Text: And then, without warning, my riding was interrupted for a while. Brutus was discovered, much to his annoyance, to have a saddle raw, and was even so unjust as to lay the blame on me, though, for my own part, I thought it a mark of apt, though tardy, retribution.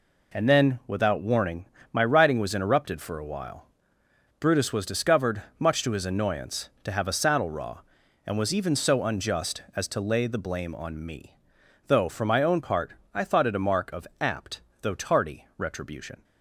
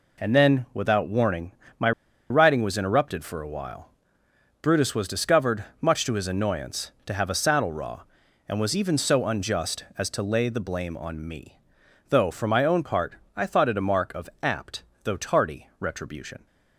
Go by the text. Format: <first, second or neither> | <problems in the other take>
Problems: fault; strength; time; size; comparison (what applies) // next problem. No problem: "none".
first | pauses between "my" and "riding"; at 1.9 s; 0.39 s long